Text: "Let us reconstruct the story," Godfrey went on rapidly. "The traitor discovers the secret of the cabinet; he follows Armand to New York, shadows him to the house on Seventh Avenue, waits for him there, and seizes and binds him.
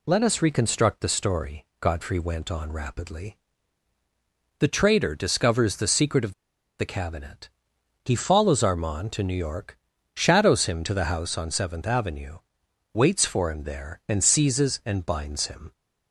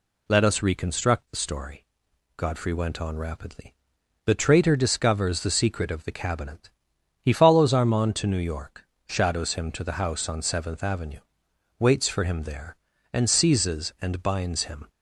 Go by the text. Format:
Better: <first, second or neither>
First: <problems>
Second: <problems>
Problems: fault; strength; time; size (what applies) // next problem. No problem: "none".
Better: second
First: pauses between "of" and "the"; noticeable; at 6.3 s; 0.46 s long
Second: none